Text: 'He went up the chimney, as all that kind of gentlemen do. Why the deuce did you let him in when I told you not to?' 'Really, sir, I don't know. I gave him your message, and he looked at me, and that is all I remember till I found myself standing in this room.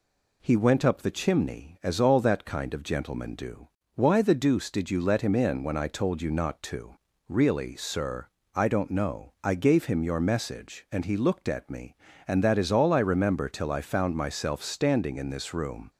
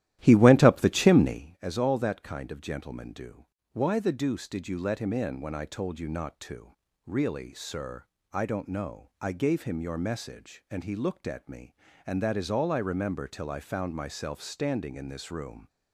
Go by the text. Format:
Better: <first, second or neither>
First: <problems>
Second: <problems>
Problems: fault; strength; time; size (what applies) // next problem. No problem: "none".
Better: first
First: none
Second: starts louder than the rest; strong; until 1.6 s; 13.5 dB